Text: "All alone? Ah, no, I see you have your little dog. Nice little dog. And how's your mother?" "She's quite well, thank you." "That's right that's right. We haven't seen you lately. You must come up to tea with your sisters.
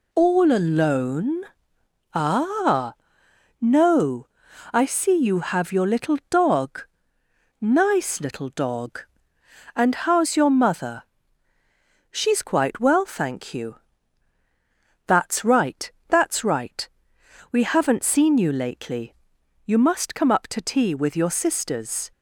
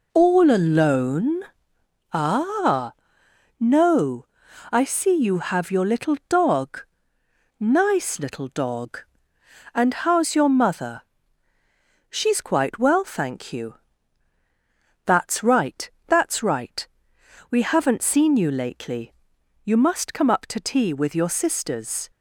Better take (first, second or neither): first